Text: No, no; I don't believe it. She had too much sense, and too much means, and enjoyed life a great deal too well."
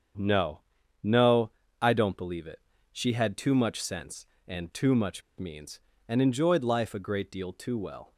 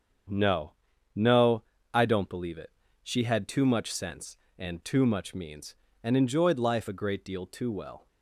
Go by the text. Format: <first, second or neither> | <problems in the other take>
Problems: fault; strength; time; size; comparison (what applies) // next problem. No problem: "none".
second | starts louder than the rest; strong; until 1.9 s; 7.5 dB; strong in the second // pauses between "much" and "means"; slight; at 5.2 s; 0.15 s long